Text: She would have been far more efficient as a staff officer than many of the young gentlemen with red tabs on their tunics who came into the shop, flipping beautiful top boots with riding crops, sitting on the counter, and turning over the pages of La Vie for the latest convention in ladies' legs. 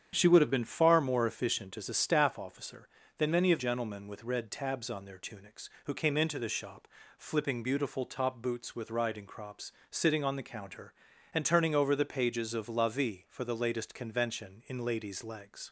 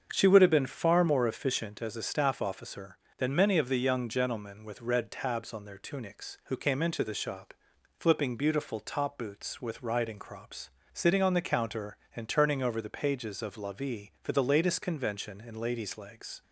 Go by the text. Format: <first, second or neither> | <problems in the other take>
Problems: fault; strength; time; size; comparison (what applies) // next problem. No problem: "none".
second | starts louder than the rest; strong; until 1.1 s; 8.5 dB; also in the second // skips "the young"; at 3.5 s